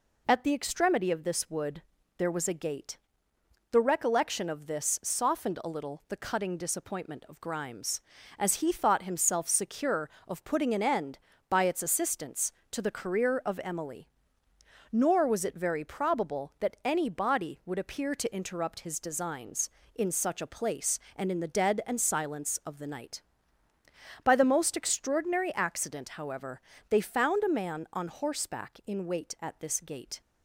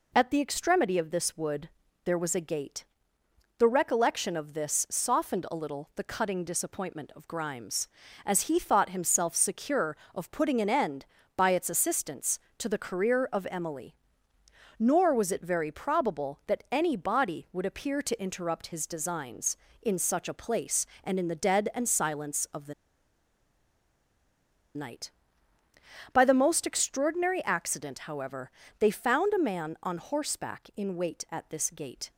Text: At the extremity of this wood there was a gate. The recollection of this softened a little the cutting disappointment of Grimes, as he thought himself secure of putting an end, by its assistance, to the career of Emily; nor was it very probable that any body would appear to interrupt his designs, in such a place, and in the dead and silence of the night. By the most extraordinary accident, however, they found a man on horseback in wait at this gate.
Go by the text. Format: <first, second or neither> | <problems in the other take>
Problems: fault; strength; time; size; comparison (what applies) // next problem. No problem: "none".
first | pauses between "wood" and "there"; slight; at 1.6 s; 0.36 s long; slight in the first // pauses between "the" and "night"; strong; at 22.7 s; 2.0 s long